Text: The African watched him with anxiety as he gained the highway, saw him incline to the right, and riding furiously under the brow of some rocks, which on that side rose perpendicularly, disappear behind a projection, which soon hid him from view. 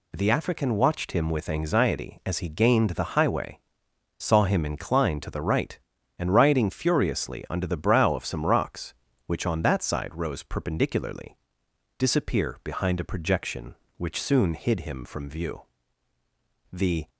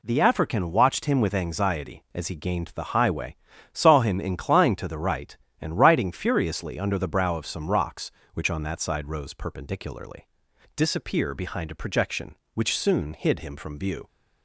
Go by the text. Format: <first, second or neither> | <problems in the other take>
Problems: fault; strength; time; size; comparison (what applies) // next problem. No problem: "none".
second | goes on to say "The"; slight; from 16.7 s on; 0.36 s long